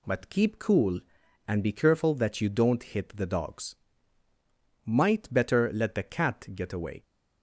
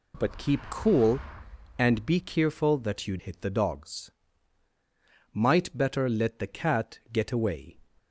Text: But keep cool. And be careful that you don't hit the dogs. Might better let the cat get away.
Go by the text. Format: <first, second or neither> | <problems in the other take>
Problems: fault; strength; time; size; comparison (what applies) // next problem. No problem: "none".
first | skips "don't"; at 3.1 s